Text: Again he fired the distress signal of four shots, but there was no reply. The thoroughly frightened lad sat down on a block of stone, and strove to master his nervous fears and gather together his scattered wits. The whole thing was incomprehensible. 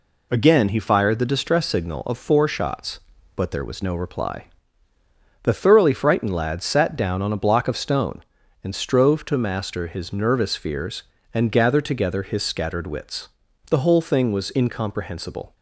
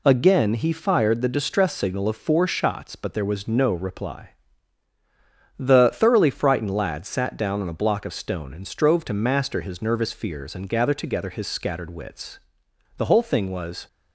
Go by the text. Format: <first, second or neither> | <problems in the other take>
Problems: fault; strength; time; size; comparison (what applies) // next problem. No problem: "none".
first | stops before "incomprehensible"; at 13.8 s